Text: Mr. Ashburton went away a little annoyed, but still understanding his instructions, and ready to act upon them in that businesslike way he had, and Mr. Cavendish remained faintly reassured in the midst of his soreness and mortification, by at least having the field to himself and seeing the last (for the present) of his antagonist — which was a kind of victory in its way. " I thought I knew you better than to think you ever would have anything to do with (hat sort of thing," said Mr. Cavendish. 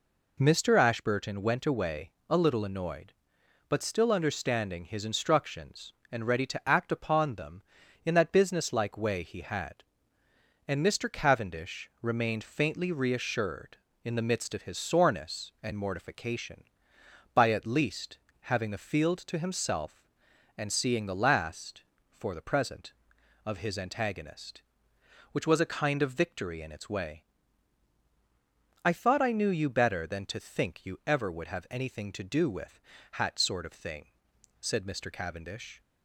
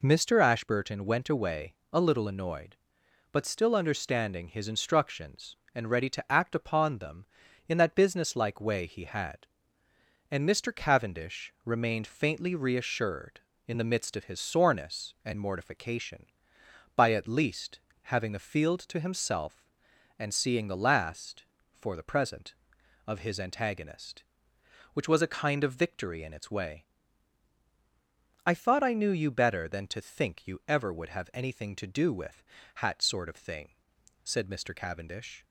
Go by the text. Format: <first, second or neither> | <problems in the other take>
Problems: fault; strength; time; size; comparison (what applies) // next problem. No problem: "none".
neither | pauses between "away" and "a"; slight; the same in both // pauses between "least" and "having"; slight; the same in both